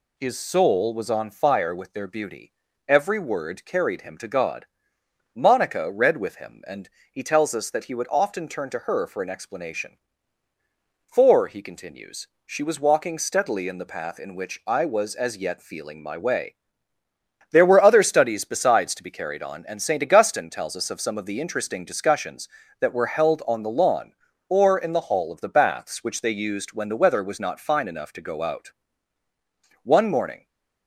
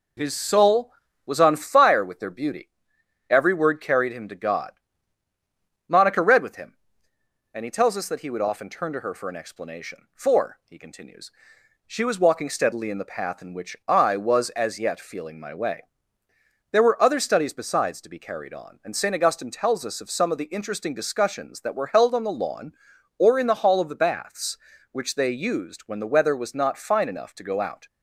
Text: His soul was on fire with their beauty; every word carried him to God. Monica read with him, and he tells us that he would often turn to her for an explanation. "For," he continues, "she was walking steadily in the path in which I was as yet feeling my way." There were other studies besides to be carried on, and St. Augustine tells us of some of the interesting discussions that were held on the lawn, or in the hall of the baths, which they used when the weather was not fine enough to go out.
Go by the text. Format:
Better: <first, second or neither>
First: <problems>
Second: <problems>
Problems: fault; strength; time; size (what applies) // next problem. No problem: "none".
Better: second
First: pauses between "and" and "he"; slight; at 6.8 s; 0.22 s long // goes on to say "One morning"; noticeable; from 29.8 s on; 0.64 s long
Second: none